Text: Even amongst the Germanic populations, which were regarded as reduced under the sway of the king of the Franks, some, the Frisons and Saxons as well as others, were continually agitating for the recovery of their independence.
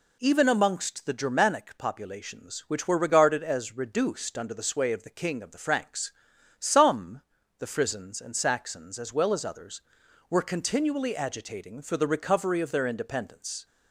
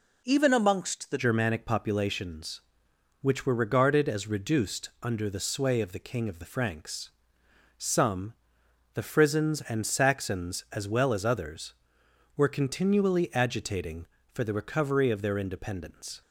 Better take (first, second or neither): first